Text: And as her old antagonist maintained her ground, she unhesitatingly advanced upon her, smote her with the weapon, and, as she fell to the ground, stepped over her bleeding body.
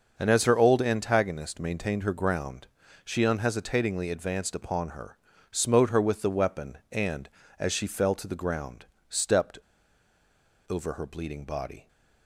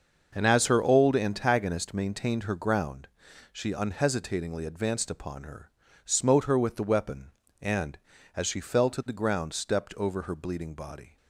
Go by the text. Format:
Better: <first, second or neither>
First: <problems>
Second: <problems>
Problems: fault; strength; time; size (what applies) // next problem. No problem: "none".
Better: second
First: starts louder than the rest; until 1.1 s; 6 dB // pauses between "stepped" and "over"; at 9.5 s; 1.1 s long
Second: starts louder than the rest; until 1.3 s; 6 dB